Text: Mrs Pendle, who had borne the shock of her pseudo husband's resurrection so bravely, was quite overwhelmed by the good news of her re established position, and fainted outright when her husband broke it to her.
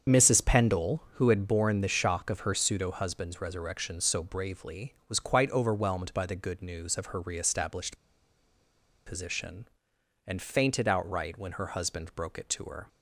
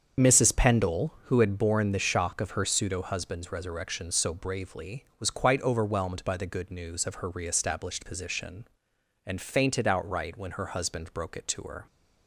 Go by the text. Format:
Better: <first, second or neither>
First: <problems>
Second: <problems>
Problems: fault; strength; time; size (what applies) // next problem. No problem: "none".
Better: second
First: starts louder than the rest; strong; until 1.2 s; 7 dB // pauses between "established" and "position"; at 7.9 s; 1.1 s long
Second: starts louder than the rest; until 1.3 s; 7 dB